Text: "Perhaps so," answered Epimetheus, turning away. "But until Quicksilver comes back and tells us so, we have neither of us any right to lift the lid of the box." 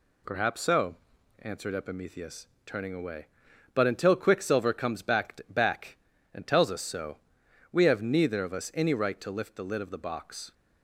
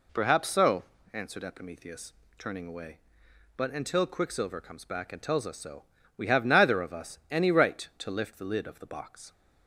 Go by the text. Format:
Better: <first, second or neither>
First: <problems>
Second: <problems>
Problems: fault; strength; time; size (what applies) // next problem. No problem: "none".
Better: second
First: says "back" twice; at 5.5 s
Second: none